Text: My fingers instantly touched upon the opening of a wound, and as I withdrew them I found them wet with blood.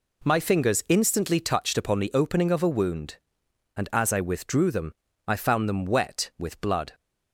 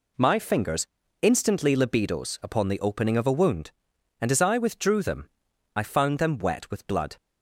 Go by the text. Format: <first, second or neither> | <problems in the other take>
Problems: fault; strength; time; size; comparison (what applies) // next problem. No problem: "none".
first | pauses between "fingers" and "instantly"; slight; at 0.8 s; 0.36 s long // says "libidos" for "touched"; at 1.7 s // pauses between "them" and "I"; noticeable; at 5.2 s; 0.46 s long; slight in the first